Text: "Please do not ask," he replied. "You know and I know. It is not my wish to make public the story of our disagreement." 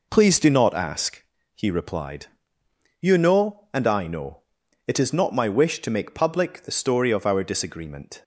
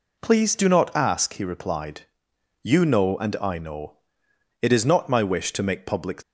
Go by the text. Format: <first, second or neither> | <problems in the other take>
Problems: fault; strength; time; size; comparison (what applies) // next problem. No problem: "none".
first | stops before "the story of our disagreement"; at 6.2 s